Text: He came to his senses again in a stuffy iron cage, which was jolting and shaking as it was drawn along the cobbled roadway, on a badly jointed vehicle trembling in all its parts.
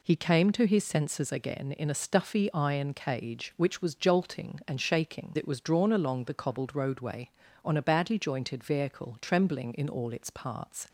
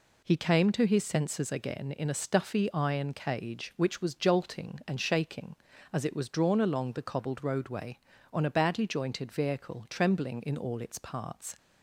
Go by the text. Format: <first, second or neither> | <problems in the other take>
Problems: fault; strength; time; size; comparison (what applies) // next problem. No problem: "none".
second | skips "as"; at 5.3 s